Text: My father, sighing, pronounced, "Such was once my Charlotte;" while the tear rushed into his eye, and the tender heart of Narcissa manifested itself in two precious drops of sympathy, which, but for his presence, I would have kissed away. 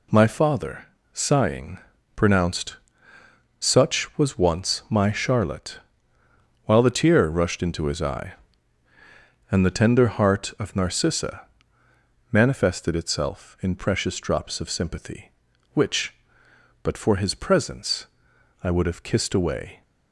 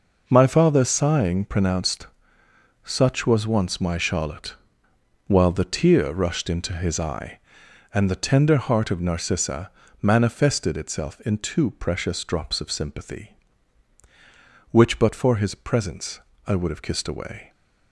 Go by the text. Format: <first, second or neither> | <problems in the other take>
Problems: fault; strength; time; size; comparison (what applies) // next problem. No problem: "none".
second | pauses between "Narcissa" and "manifested"; noticeable; at 11.4 s; 0.86 s long; slight in the second // skips "two"; at 13.7 s